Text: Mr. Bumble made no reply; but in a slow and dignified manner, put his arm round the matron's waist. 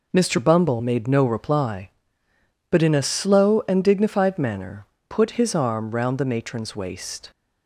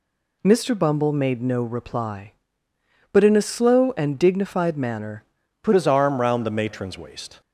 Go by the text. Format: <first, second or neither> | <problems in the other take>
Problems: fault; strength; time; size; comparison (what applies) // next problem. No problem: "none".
first | changes voice at "his"; from 5.7 s on; 1.7 s long